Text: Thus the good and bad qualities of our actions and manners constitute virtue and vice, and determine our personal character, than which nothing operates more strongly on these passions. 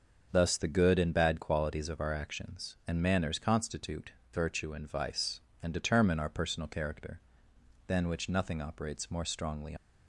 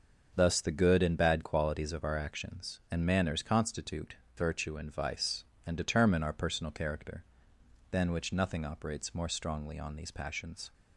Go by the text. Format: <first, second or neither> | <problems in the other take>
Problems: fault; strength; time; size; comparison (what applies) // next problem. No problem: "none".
second | starts louder than the rest; until 1.3 s; 6.5 dB; also in the second // pauses between "constitute" and "virtue"; slight; at 4.1 s; 0.20 s long; slight in the second // stops before "on these passions"; at 9.7 s